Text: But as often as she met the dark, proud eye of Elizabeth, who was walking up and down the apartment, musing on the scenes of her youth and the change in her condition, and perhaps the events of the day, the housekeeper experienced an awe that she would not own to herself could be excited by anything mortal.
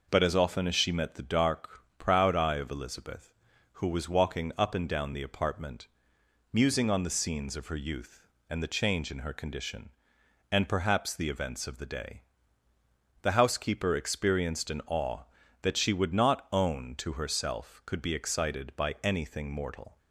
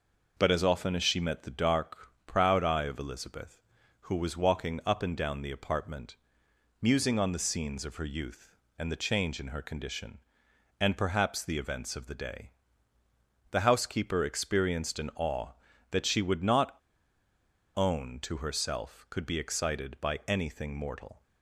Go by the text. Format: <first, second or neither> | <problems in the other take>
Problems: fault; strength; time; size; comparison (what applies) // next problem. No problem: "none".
first | pauses between "not" and "own"; at 16.7 s; 1.0 s long